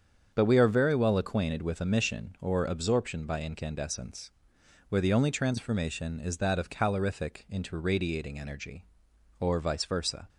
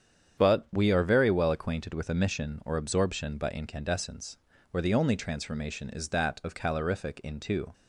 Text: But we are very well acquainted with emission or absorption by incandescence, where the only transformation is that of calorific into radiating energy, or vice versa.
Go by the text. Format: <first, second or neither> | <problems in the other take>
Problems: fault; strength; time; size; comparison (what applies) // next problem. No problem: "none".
first | starts louder than the rest; strong; until 1.4 s; 8 dB; strong in the first // stops before "radiating energy or vice versa"; at 7.7 s